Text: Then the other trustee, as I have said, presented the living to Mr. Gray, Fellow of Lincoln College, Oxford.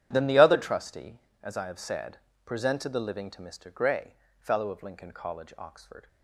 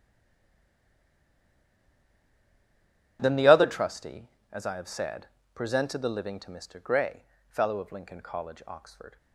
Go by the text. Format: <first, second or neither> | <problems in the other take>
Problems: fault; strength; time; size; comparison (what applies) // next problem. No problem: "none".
first | stays silent before the first word; strong; until 3.1 s; 3.1 s long // starts louder than the rest; strong; until 4.2 s; 10.5 dB; strong in the first